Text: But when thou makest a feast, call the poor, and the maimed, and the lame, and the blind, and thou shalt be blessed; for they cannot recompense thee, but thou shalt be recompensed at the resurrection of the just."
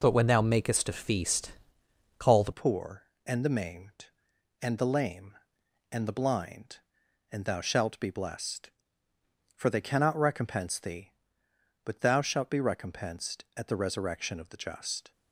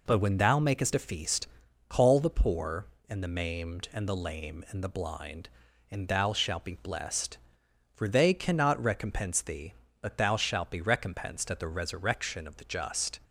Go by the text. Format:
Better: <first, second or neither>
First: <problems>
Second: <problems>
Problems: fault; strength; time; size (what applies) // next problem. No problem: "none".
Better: second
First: changes voice at "poor"; from 2.5 s on; 12.6 s long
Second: none